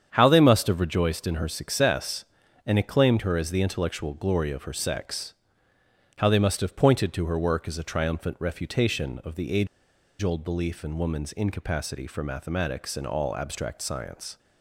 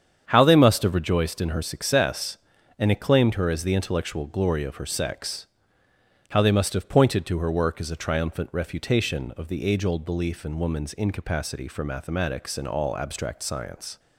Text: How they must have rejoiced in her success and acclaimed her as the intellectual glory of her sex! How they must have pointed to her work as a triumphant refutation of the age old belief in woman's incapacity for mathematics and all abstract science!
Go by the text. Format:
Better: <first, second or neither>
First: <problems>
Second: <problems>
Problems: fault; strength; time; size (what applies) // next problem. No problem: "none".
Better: second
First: starts louder than the rest; strong; until 1.1 s; 8 dB // pauses between "age" and "old"; noticeable; at 9.6 s; 0.54 s long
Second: starts louder than the rest; strong; until 1.3 s; 8 dB